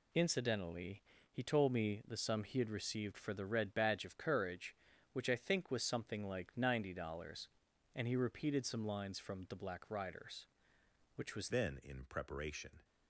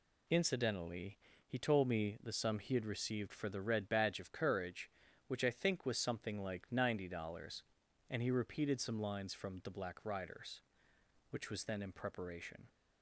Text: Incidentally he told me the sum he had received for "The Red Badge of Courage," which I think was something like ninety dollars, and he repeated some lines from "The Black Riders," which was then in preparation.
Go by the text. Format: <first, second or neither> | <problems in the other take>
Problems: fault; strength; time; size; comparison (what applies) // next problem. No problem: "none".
second | pauses between "Incidentally" and "he"; slight; at 1.0 s; 0.30 s long; slight in the second // changes voice at "then"; from 11.5 s on; 1.3 s long